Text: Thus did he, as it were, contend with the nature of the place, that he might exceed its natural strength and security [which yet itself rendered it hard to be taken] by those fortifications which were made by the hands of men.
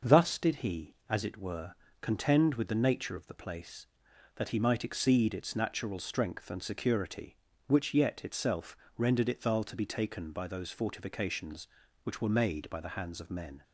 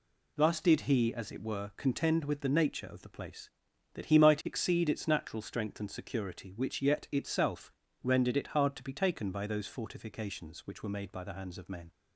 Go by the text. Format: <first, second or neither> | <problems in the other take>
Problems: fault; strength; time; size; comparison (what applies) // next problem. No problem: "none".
second | starts louder than the rest; until 1.1 s; 6 dB // pauses between "itself" and "rendered"; slight; at 8.7 s; 0.22 s long; slight in the second // says "thal" for "hard"; at 9.4 s